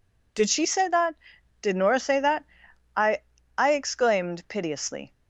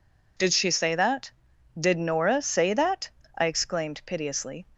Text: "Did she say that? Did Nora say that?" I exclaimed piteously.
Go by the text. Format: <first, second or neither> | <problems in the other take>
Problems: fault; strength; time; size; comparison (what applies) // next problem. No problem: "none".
second | says "I" twice; at 3.5 s